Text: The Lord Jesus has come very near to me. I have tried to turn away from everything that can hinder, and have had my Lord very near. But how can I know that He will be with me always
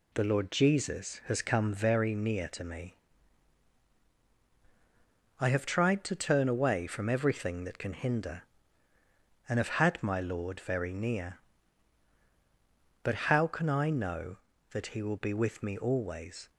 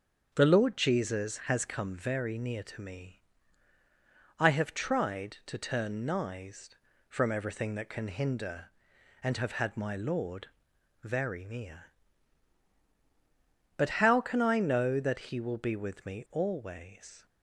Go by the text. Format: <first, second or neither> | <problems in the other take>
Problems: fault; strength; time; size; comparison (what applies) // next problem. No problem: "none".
first | starts louder than the rest; until 1.3 s; 7 dB // says "nised" for "away"; at 6.0 s // pauses between "Lord" and "very"; noticeable; at 10.4 s; 0.58 s long